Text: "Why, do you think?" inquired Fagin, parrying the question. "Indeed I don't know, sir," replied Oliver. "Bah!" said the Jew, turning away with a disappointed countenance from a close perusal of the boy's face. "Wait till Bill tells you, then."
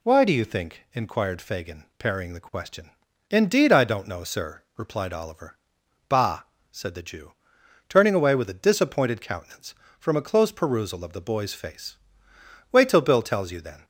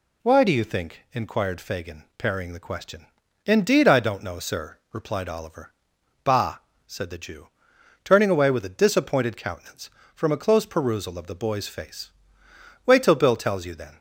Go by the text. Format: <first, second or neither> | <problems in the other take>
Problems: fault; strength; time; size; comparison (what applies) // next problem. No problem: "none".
neither | none